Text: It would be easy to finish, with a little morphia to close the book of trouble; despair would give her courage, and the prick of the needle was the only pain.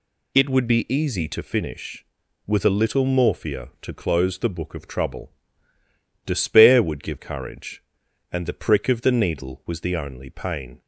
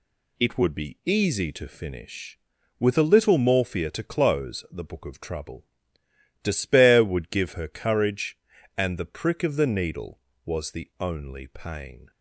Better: second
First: skips "her"; at 7.1 s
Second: none

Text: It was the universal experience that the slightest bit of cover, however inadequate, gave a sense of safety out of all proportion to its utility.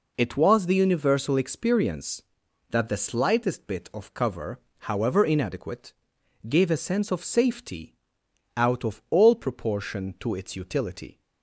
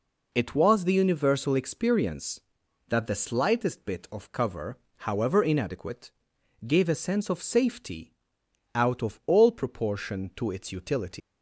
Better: first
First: pauses between "safety" and "out"; noticeable; at 7.9 s; 0.62 s long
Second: pauses between "safety" and "out"; noticeable; at 8.1 s; 0.62 s long // leaves "utility" unfinished; at 11.2 s; 160 ms

